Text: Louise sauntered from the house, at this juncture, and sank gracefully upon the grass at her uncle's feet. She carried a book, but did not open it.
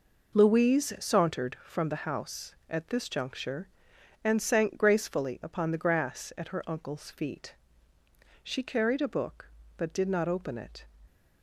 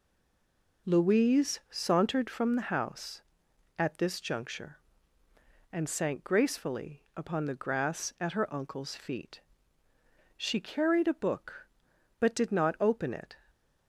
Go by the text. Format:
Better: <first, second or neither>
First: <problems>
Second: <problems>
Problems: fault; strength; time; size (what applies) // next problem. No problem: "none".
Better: first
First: none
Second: stays silent before the first word; slight; until 0.8 s; 0.8 s long